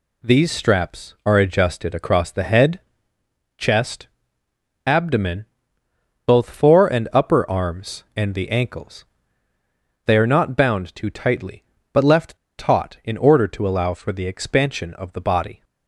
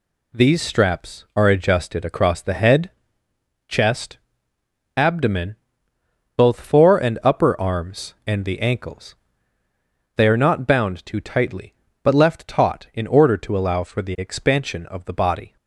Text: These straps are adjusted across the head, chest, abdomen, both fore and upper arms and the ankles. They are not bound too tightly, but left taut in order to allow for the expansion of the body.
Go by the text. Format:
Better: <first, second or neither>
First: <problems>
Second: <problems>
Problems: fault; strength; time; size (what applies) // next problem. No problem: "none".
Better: second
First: pauses between "left" and "taut"; slight; at 12.3 s; 0.21 s long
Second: none